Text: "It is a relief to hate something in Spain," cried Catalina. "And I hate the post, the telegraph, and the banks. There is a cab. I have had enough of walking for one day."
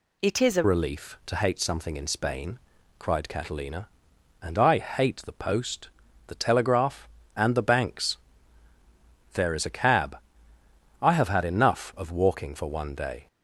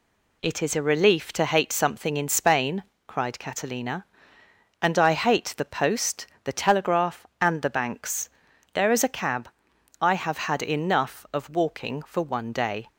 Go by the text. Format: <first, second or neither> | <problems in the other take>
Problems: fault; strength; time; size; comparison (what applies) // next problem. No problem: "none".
second | changes voice at "relief"; from 0.6 s on; 12.6 s long